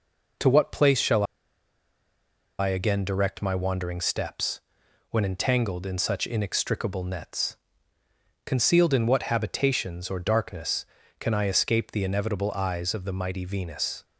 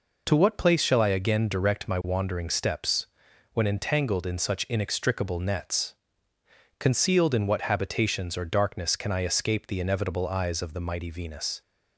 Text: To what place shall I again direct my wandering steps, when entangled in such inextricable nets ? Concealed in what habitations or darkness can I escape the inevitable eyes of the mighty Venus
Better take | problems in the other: second | pauses between "shall" and "I"; strong; at 1.2 s; 1.3 s long

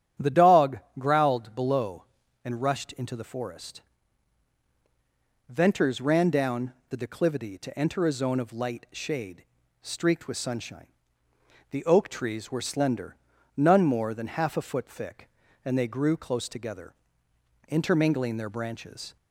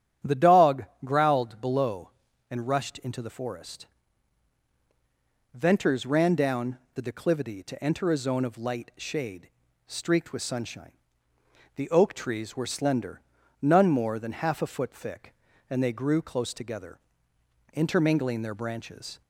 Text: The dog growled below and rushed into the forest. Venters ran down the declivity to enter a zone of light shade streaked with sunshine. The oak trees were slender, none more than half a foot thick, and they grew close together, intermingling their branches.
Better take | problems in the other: neither | starts louder than the rest; strong; the same in both // pauses between "dog" and "growled"; slight; the same in both // pauses between "down" and "the"; slight; the same in both // pauses between "shade" and "streaked"; the same in both

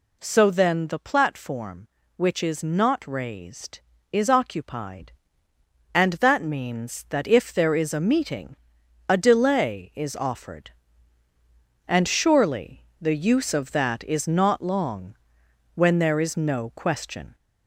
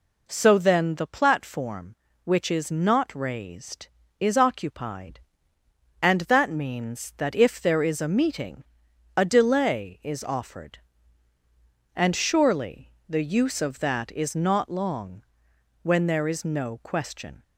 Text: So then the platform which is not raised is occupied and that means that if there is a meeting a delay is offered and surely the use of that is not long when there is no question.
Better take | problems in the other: second | gets louder; slight; throughout; 2.5 dB // pauses between "meeting" and "a"; noticeable; at 8.5 s; 0.52 s long; noticeable in the second // pauses between "surely" and "the"; slight; at 12.8 s; 0.18 s long; slight in the second // pauses between "long" and "when"; noticeable; at 15.1 s; 0.60 s long; noticeable in the second

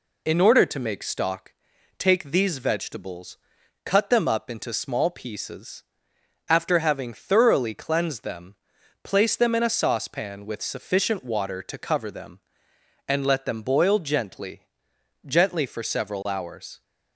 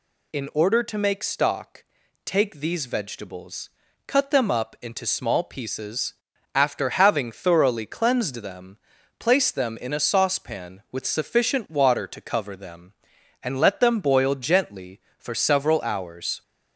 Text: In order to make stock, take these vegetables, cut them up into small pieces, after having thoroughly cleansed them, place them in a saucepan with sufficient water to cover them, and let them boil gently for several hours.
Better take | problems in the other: second | says "gently" twice; at 15.2 s

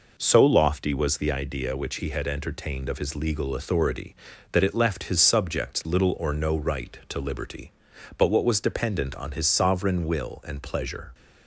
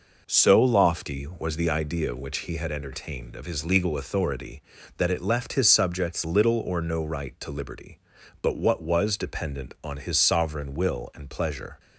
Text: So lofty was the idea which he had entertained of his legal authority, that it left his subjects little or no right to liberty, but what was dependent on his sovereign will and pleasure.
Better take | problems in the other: neither | none

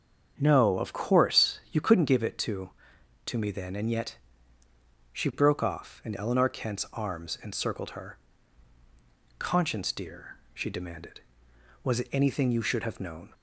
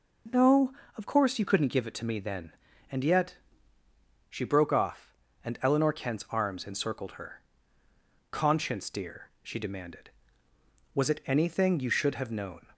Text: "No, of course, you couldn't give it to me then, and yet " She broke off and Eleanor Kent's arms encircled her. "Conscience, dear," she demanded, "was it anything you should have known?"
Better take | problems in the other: second | starts louder than the rest; strong; until 1.3 s; 7.5 dB // says "to" twice; at 3.2 s

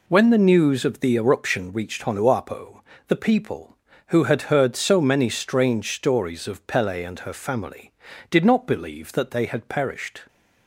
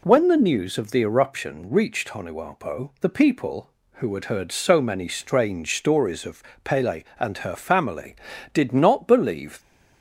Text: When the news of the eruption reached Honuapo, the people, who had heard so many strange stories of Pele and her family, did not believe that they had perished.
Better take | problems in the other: first | pauses between "of" and "Pele"; slight; at 6.4 s; 0.20 s long // stops before "that they had perished"; at 9.6 s

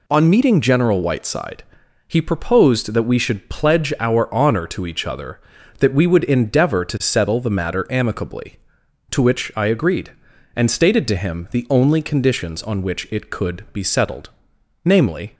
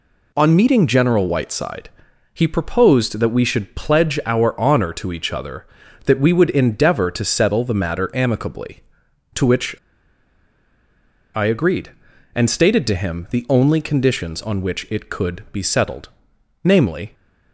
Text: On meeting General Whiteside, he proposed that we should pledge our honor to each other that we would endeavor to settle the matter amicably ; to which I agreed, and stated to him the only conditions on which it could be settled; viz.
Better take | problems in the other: first | pauses between "which" and "I"; strong; at 9.7 s; 1.5 s long

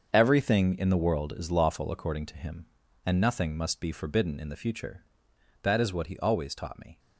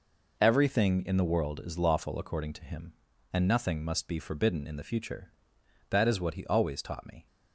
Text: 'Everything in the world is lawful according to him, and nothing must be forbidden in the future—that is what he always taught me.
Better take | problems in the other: second | gets quieter; strong; throughout; 11.5 dB

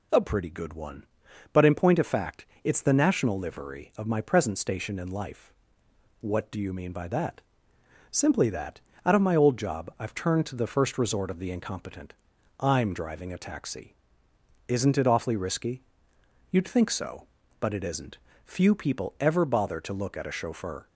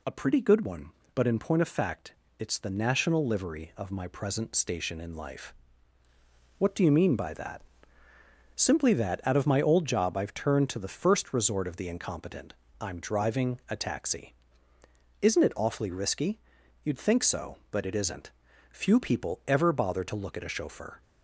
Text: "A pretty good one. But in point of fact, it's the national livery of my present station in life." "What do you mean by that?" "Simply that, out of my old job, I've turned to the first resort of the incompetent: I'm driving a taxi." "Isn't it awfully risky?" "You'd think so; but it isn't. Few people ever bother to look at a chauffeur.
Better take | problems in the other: neither | none

